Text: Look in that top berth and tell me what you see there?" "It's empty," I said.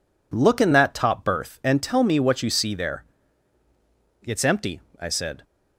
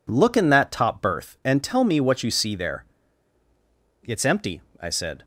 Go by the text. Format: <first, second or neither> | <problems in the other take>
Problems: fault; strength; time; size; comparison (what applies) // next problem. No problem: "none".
neither | none